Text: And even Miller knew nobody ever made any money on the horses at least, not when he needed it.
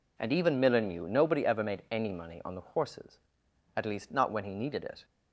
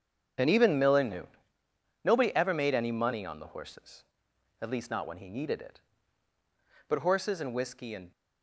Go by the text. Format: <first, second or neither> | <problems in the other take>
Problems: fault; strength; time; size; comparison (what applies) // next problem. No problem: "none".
first | starts louder than the rest; strong; until 2.1 s; 8 dB // pauses between "knew" and "nobody"; noticeable; at 1.2 s; 0.78 s long // goes on to say "But horses and whiskey and"; noticeable; from 6.8 s on; 1.2 s long